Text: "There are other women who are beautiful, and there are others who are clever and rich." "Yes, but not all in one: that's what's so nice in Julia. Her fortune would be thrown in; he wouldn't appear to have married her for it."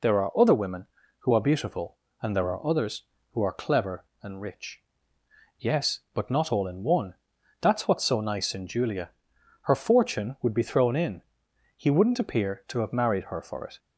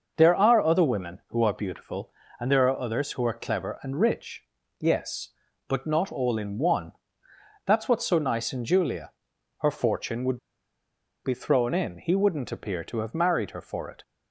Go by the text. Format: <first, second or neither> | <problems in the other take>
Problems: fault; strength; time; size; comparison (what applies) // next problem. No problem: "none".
first | starts louder than the rest; noticeable; until 1.1 s; 6 dB // pauses between "would" and "be"; noticeable; at 10.3 s; 0.87 s long